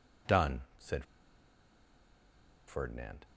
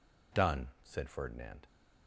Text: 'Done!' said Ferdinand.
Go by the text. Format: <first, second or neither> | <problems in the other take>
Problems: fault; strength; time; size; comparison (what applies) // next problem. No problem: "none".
second | pauses between "said" and "Ferdinand"; strong; at 1.0 s; 1.6 s long